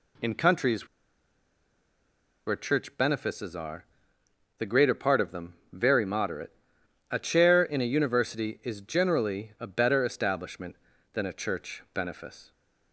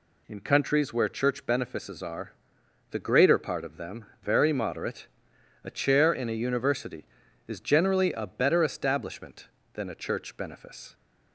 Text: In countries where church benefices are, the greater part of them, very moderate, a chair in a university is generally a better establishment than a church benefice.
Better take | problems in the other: second | pauses between "countries" and "where"; strong; at 0.8 s; 1.6 s long

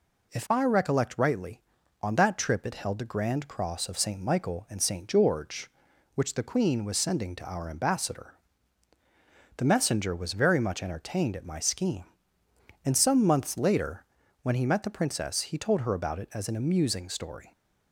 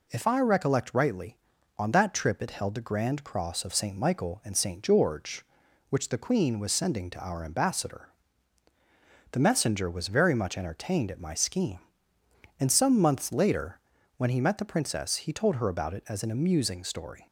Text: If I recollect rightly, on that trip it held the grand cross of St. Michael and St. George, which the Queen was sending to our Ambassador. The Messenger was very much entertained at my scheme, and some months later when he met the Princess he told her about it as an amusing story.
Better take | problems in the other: neither | pauses between "later" and "when"; slight; the same in both

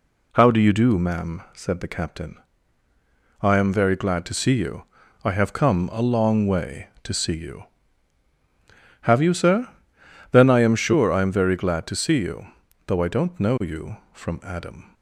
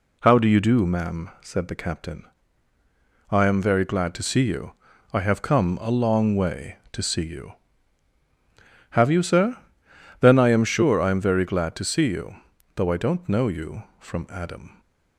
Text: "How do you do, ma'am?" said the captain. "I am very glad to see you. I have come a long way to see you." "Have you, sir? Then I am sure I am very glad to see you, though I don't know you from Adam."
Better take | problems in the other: neither | none

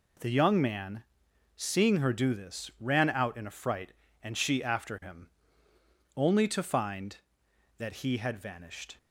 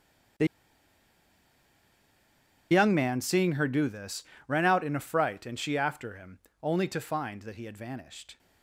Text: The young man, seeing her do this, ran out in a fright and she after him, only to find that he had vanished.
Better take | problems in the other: first | starts louder than the rest; strong; until 3.6 s; 9.5 dB // pauses between "The" and "young"; strong; at 0.4 s; 2.2 s long

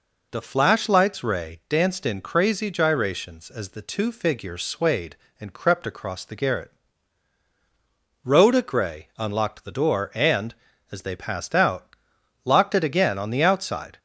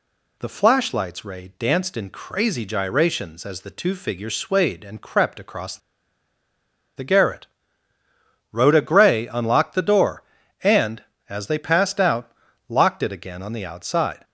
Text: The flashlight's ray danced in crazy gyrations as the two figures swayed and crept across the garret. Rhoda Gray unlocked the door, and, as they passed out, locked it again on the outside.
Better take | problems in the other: first | pauses between "across" and "the"; at 5.7 s; 1.1 s long

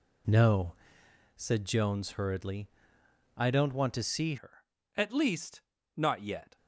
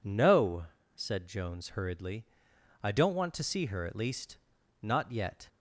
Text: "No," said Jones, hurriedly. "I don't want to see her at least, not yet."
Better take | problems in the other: second | changes voice at "her"; from 4.3 s on; 2.2 s long

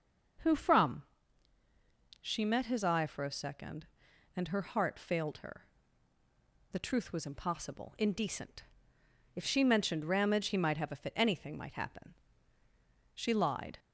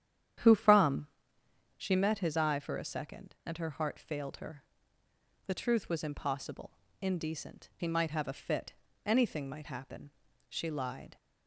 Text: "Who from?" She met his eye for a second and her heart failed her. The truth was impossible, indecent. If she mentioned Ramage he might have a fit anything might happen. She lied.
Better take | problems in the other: first | starts louder than the rest; strong; until 2.1 s; 10 dB // skips "If she mentioned Ramage"; at 7.7 s // pauses between "fit" and "anything"; slight; at 8.7 s; 0.32 s long

